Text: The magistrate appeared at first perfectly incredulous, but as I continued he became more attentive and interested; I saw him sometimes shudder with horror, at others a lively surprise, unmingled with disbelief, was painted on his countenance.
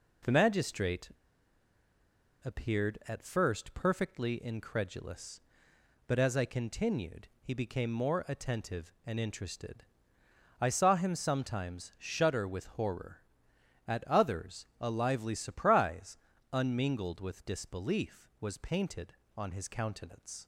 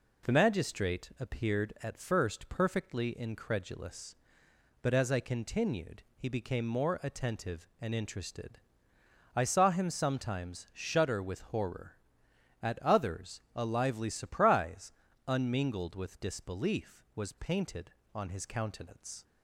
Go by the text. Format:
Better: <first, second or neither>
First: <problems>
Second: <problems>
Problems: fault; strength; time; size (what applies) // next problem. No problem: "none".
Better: second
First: pauses between "magistrate" and "appeared"; strong; at 1.0 s; 1.3 s long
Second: none